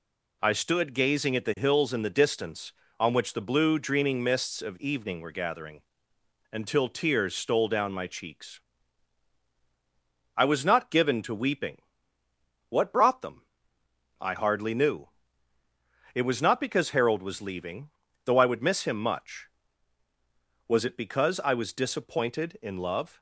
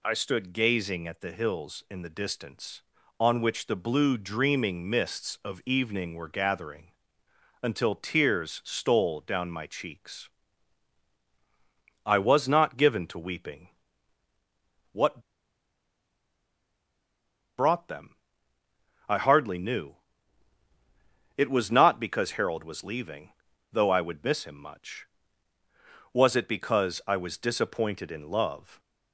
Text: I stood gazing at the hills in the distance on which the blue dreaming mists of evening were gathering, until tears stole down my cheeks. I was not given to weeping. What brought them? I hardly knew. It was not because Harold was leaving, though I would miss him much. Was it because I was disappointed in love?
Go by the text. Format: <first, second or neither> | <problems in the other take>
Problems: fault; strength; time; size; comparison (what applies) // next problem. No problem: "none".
first | pauses between "What" and "brought"; strong; at 15.2 s; 2.3 s long